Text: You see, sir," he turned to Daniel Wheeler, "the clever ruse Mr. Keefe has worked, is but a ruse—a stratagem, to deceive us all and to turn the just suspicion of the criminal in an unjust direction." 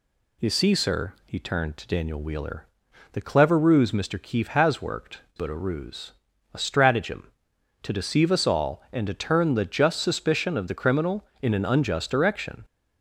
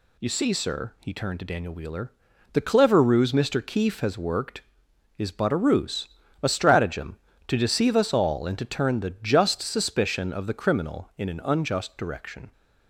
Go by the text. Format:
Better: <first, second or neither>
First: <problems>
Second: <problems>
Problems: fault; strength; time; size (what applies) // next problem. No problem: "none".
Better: second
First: skips "is"; at 5.2 s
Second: none